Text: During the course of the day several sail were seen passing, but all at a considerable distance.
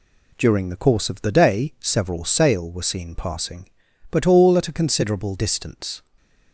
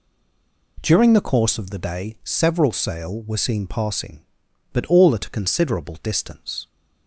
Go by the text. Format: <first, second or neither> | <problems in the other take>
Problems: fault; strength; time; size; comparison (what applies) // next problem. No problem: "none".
first | stays silent before the first word; slight; until 0.7 s; 0.7 s long